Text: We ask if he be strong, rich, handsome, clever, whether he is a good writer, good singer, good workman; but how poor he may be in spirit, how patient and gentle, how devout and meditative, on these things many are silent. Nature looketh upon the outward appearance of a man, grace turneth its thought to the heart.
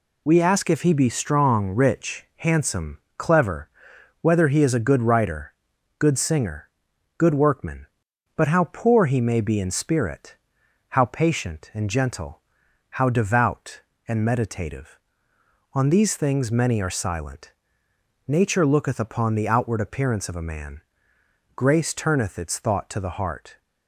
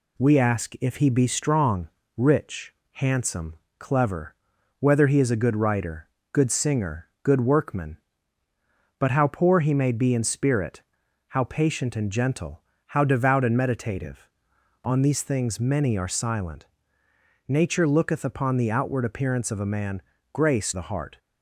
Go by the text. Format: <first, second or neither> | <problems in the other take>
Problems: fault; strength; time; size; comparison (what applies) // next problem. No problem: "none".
first | skips "turneth its thought to"; at 20.7 s